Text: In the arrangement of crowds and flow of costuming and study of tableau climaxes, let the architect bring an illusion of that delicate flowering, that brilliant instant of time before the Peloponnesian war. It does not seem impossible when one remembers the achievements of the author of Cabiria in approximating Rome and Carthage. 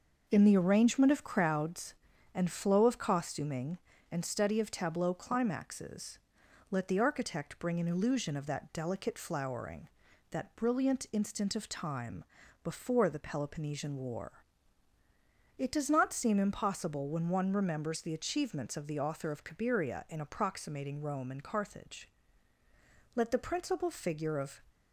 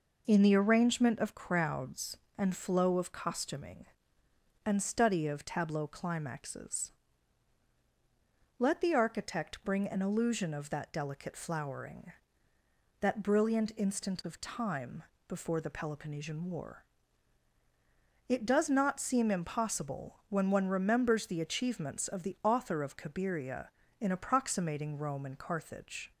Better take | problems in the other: second | pauses between "time" and "before"; at 12.2 s; 0.40 s long; slight in the second // goes on to say "Let the principal figure of"; from 23.1 s on; 1.4 s long

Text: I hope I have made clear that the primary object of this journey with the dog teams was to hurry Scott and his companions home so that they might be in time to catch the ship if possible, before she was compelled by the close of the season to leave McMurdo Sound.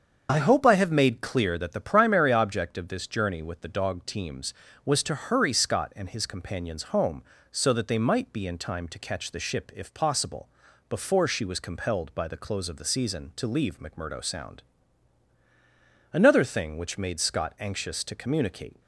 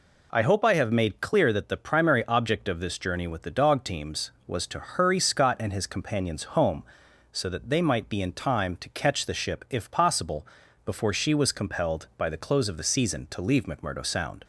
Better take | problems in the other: second | starts louder than the rest; strong; until 1.3 s; 7 dB // goes on to say "Another thing which made Scott anxious to communicate"; strong; from 16.1 s on; 2.6 s long

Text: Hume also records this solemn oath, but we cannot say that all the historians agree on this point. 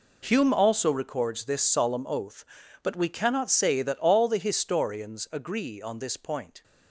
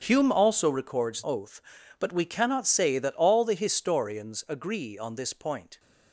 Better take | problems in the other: first | starts louder than the rest; strong; until 1.0 s; 7 dB // skips "this solemn"; at 1.2 s

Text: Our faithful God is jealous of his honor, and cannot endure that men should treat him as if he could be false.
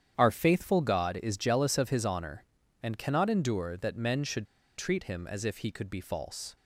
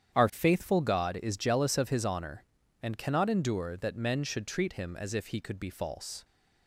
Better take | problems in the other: second | starts louder than the rest; strong; until 1.1 s; 9 dB; strong in the second // pauses between "should" and "treat"; slight; at 4.4 s; 0.31 s long

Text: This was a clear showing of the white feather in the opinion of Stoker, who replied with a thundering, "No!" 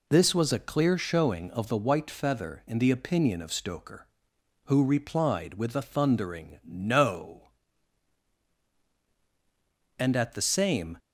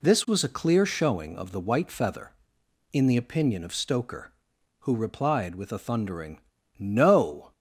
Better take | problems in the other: second | goes on to say "and at the same"; noticeable; from 9.9 s on; 1.0 s long

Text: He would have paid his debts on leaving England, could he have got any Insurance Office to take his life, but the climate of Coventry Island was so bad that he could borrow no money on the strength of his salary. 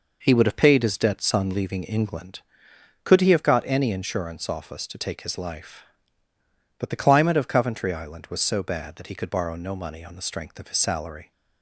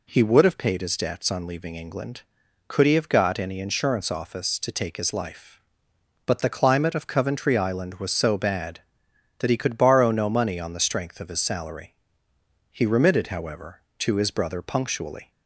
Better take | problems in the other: first | goes on to say "He remitted however to his brother punctually"; strong; from 12.7 s on; 2.6 s long

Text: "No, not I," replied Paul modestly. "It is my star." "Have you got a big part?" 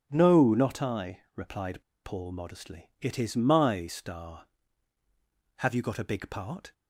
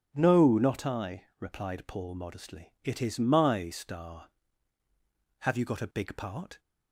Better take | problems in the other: second | starts louder than the rest; until 1.1 s; 6.5 dB; noticeable in the second // pauses between "replied" and "Paul"; slight; at 1.8 s; 0.22 s long

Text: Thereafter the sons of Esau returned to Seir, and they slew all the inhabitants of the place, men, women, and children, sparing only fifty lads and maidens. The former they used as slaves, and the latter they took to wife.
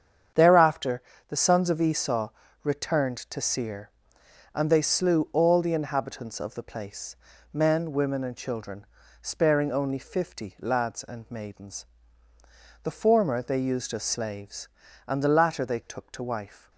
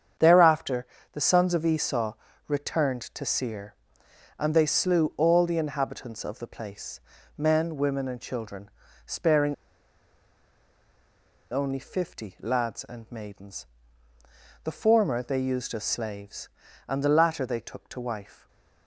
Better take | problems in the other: first | starts louder than the rest; strong; until 1.4 s; 8 dB; strong in the first // pauses between "Thereafter" and "the"; slight; at 0.8 s; 0.26 s long; slight in the first // pauses between "Esau" and "returned"; slight; at 2.1 s; 0.34 s long; slight in the first // pauses between "sparing" and "only"; strong; at 9.5 s; 1.9 s long

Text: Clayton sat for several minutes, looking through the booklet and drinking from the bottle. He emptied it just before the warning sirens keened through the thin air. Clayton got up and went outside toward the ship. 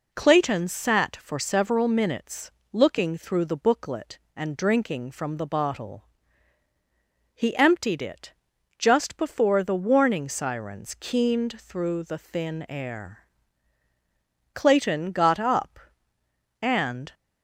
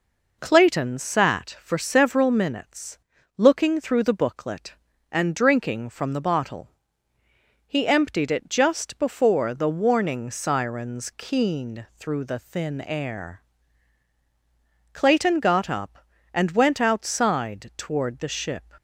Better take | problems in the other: second | pauses between "it" and "just"; at 8.3 s; 0.44 s long // stops before "went outside toward the ship"; at 17.1 s

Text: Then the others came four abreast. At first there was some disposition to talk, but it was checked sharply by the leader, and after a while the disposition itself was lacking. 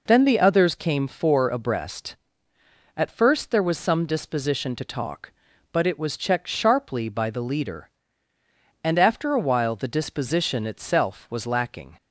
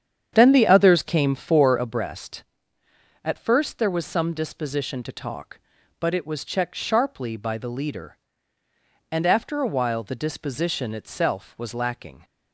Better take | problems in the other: first | starts louder than the rest; strong; until 2.0 s; 8.5 dB

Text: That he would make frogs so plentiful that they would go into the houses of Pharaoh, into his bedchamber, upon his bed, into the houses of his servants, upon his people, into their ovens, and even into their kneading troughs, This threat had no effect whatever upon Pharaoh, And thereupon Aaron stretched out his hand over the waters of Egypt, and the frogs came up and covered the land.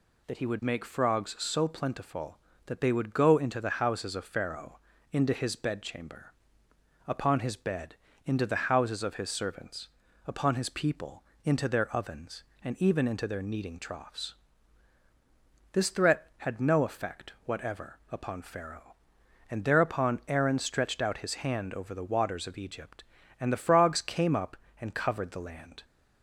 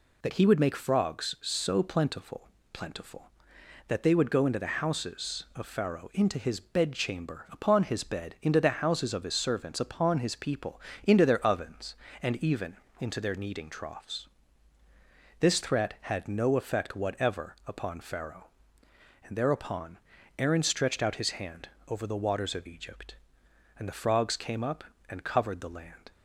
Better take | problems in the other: first | says "plentiful" twice; at 2.7 s // pauses between "even" and "into"; slight; at 12.7 s; 0.24 s long // pauses between "thereupon" and "Aaron"; at 19.9 s; 0.40 s long // pauses between "hand" and "over"; slight; at 21.6 s; 0.22 s long

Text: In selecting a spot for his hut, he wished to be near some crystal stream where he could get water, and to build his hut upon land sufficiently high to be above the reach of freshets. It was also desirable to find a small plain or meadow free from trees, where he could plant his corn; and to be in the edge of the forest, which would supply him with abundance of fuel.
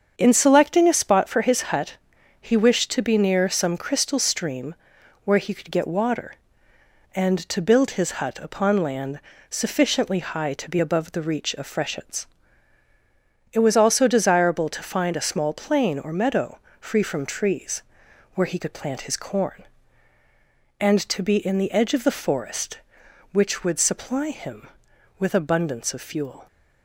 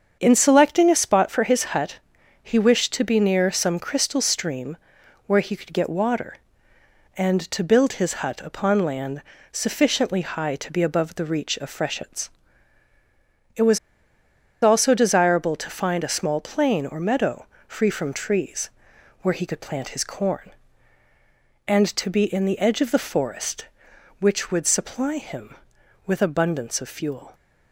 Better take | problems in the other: first | starts louder than the rest; strong; until 1.2 s; 7 dB; strong in the first // pauses between "stream" and "where"; noticeable; at 4.7 s; 0.50 s long; noticeable in the first // pauses between "land" and "sufficiently"; slight; at 9.2 s; 0.28 s long; slight in the first // pauses between "was" and "also"; noticeable; at 13.7 s; 0.85 s long // pauses between "meadow" and "free"; slight; at 17.4 s; 0.22 s long; slight in the first

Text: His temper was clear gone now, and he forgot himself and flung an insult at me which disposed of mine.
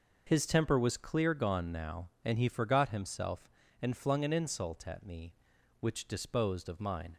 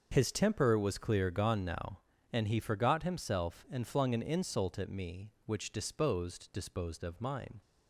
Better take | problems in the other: first | starts louder than the rest; until 1.1 s; 6.5 dB // says "disposed" twice; at 6.5 s

